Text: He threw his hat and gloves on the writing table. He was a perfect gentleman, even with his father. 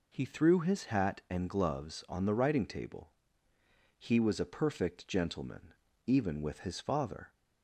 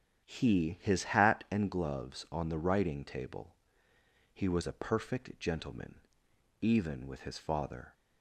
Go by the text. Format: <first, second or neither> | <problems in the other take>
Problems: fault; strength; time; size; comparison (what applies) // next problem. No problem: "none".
first | starts louder than the rest; strong; until 1.2 s; 9 dB // skips "threw"; at 0.7 s